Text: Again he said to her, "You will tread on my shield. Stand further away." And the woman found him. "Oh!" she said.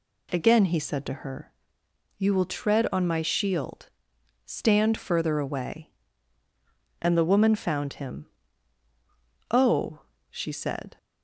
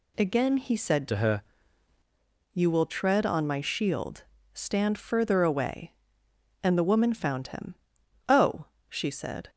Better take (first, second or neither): first